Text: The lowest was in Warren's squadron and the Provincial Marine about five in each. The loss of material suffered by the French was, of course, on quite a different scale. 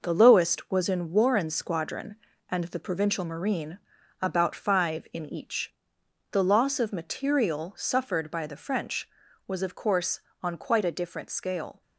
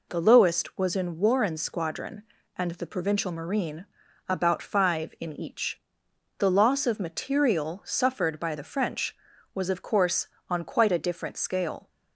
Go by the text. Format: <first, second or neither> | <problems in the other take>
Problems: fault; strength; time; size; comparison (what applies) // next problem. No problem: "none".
second | gets quieter; throughout; 7 dB // pauses between "Marine" and "about"; at 3.7 s; 0.42 s long; also in the second